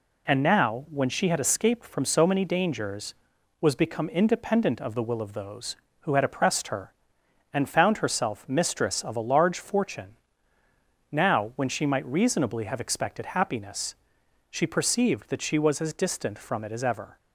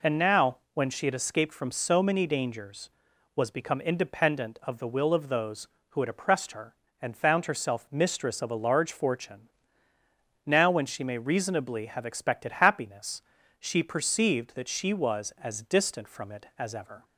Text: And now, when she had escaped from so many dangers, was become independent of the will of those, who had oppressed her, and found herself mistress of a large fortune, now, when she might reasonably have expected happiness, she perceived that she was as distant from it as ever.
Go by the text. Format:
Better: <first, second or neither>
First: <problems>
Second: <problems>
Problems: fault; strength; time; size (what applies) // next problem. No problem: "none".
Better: first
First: none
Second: says "may" for "might"; at 11.0 s